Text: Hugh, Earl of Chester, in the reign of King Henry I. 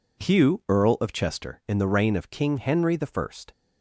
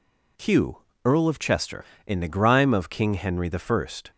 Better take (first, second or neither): first